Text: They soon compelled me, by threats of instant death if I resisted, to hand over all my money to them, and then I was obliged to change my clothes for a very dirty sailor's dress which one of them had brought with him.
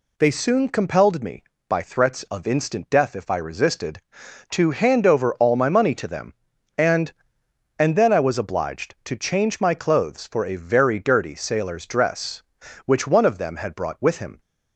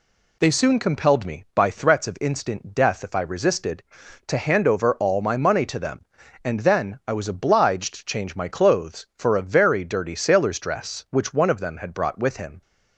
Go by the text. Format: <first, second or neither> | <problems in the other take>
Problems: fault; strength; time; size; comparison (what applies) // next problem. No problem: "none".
second | says "and" twice; at 7.7 s